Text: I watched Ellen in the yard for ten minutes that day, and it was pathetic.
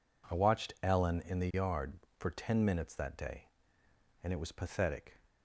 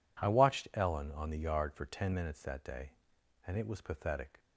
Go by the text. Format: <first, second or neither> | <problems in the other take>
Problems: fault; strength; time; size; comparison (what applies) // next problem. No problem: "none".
first | says "on" for "in"; at 1.1 s